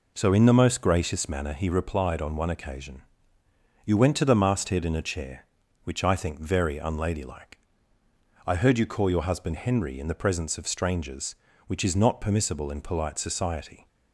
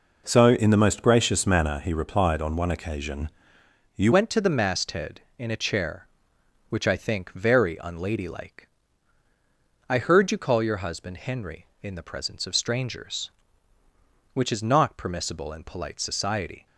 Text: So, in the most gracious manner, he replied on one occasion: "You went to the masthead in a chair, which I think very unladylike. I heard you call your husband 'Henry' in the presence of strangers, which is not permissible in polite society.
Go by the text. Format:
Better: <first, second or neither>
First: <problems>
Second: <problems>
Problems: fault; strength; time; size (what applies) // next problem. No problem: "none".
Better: first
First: none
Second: changes voice at "went"; from 4.1 s on; 12.5 s long